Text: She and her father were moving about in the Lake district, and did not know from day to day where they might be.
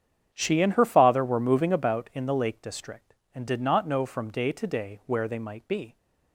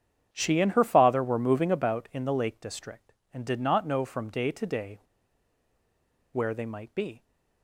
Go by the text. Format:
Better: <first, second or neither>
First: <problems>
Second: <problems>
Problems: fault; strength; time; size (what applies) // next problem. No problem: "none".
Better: first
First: starts louder than the rest; strong; until 1.3 s; 8.5 dB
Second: starts louder than the rest; strong; until 1.3 s; 8.5 dB // pauses between "day" and "where"; strong; at 5.0 s; 1.3 s long